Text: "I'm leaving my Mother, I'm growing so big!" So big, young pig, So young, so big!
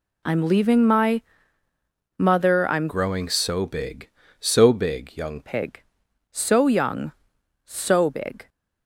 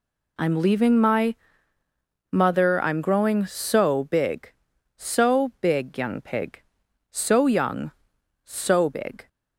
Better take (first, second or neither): second